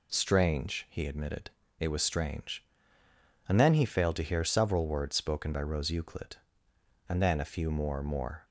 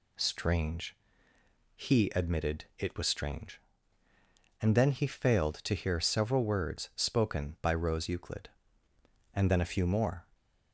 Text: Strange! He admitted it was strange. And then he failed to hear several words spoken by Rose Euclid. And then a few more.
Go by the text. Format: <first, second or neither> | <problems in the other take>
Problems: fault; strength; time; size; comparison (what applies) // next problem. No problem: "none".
second | pauses between "admitted" and "it"; slight; at 1.5 s; 0.28 s long // says "more" twice; at 8.0 s